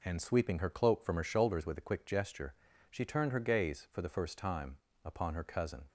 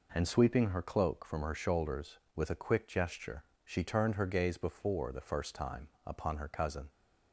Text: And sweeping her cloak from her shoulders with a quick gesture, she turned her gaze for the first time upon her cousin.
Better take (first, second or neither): first